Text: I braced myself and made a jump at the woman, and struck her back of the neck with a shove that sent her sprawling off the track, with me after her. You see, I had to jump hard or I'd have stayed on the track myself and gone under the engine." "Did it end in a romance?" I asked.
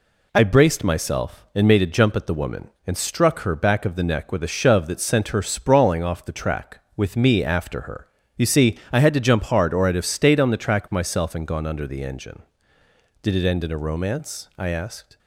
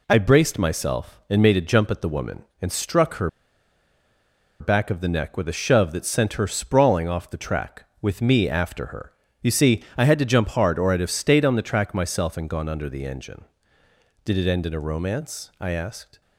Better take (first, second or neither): first